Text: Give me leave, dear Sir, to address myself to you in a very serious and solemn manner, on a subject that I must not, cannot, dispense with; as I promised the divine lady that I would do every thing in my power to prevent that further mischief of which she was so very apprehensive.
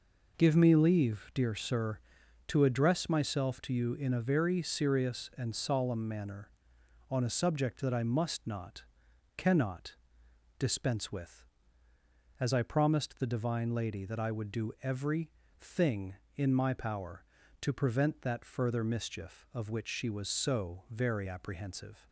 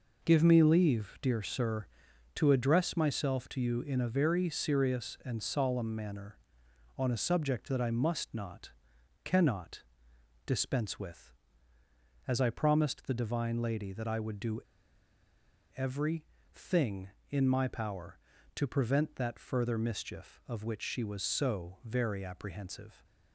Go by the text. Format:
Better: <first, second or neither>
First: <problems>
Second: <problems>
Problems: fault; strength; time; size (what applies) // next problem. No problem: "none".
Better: first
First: pauses between "every" and "thing"; slight; at 15.2 s; 0.30 s long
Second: pauses between "do" and "every"; at 14.5 s; 1.1 s long // pauses between "every" and "thing"; slight; at 16.2 s; 0.30 s long